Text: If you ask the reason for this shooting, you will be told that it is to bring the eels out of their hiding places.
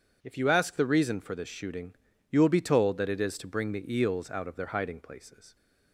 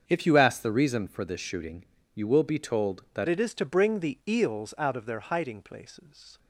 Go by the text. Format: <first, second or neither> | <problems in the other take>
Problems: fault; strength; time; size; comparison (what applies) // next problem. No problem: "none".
first | starts louder than the rest; strong; until 1.0 s; 7 dB // changes voice at "it"; from 3.2 s on; 3.1 s long